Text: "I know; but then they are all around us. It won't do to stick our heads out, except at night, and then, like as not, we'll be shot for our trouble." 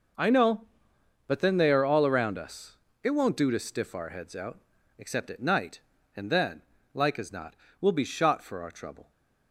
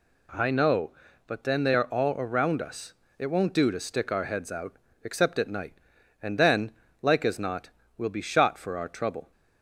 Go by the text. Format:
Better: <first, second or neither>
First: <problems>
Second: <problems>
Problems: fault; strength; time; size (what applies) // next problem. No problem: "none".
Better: second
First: says "stiff" for "stick"; at 3.5 s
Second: none